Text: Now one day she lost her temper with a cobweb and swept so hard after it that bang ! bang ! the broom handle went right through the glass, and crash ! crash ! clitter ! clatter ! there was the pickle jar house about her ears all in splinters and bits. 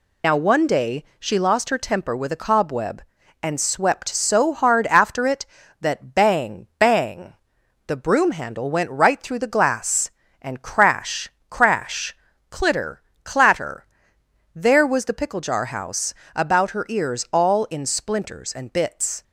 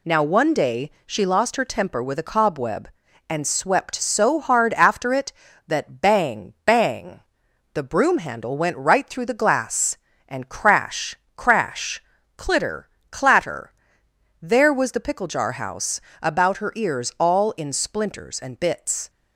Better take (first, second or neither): second